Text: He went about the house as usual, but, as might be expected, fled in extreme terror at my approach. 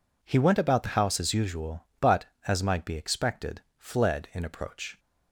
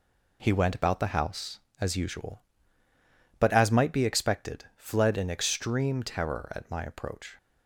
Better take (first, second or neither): second